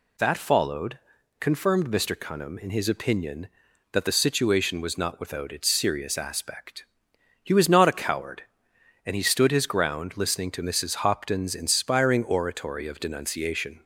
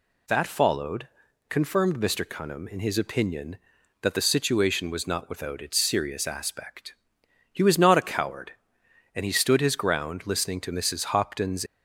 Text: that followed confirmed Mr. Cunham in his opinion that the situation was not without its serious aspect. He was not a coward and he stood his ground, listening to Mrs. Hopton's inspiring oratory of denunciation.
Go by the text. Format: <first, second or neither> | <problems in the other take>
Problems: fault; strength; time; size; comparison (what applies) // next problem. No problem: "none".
first | pauses between "followed" and "confirmed"; at 1.0 s; 0.40 s long; also in the first // stops before "inspiring oratory of denunciation"; at 11.6 s